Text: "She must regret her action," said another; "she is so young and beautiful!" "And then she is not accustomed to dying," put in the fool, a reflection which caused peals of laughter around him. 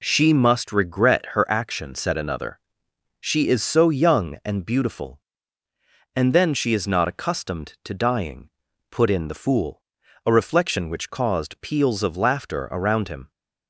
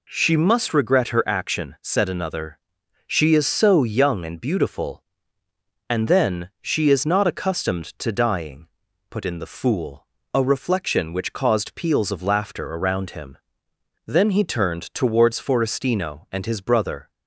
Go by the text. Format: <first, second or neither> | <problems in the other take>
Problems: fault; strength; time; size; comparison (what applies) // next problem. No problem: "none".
first | goes on to say "Then he turned towards Forestino and his brother"; strong; from 14.0 s on; 3.0 s long